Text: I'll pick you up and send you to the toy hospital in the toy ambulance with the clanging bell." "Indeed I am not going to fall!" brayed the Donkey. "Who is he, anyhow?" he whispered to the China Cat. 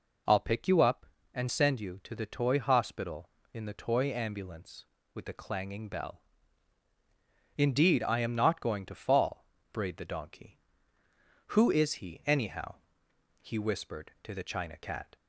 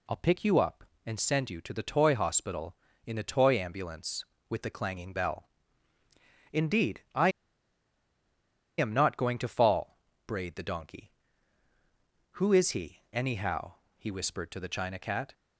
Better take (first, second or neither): first